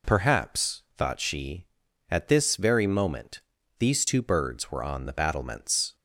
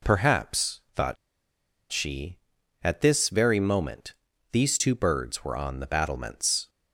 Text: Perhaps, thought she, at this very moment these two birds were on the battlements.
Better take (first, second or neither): first